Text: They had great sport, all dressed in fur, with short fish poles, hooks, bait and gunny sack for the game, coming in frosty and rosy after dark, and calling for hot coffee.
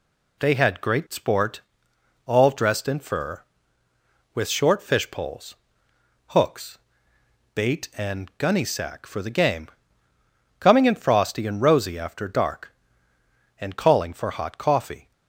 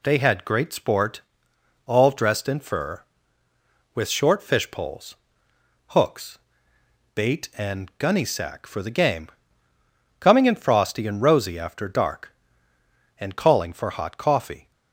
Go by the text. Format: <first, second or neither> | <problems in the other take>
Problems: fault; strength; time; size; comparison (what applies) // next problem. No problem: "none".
neither | none